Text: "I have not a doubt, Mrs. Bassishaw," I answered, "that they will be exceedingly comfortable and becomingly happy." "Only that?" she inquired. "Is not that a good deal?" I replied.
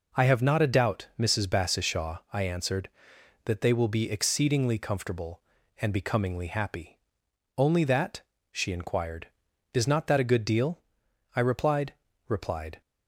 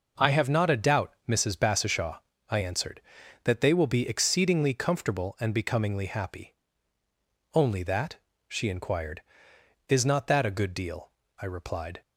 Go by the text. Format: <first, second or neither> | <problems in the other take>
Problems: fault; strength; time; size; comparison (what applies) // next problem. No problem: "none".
second | says "replied" twice; at 12.2 s